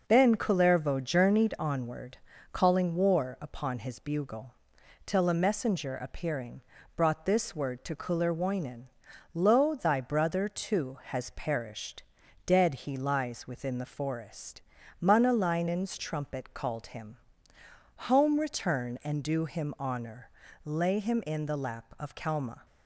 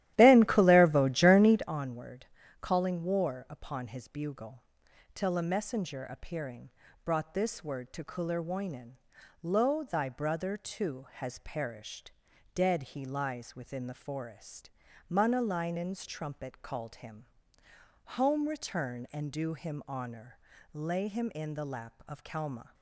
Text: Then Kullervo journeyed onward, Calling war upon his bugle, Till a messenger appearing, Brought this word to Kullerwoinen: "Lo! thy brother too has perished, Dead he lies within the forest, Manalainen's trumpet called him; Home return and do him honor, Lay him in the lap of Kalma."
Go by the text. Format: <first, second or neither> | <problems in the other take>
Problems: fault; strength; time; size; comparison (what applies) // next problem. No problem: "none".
first | starts louder than the rest; strong; until 1.8 s; 13.5 dB